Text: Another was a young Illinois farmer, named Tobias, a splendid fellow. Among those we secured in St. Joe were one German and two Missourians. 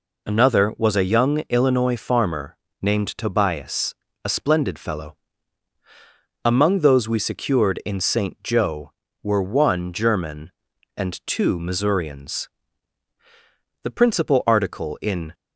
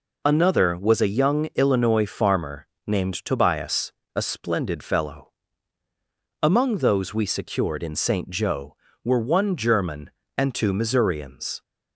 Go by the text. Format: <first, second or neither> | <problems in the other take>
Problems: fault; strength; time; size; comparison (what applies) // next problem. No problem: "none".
second | goes on to say "The principal article in"; from 13.8 s on; 1.4 s long